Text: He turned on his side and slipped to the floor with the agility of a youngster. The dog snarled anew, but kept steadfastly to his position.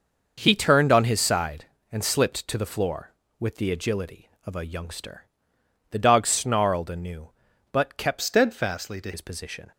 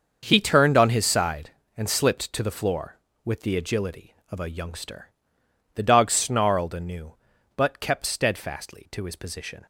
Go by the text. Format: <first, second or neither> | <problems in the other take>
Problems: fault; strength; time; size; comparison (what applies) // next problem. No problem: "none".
second | starts louder than the rest; noticeable; until 1.3 s; 6 dB; also in the second // changes voice from "steadfastly" to "to"; from 8.2 to 9.1 s; 0.9 s long